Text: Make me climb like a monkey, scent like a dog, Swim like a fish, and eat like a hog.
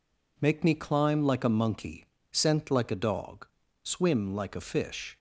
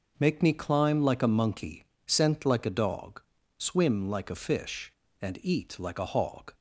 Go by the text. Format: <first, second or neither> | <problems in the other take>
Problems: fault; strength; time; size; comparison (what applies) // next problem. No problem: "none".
second | stops before "and eat like a hog"; at 5.1 s